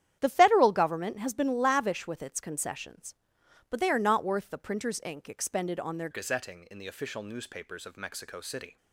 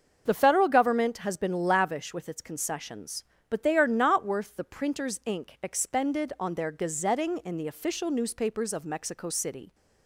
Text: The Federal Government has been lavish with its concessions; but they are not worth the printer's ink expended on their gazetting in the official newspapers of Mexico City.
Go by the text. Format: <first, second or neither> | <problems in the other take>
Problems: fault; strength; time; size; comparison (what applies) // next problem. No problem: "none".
second | starts louder than the rest; strong; until 1.2 s; 10 dB; also in the second // changes voice at "gazetting"; from 6.1 s on; 2.6 s long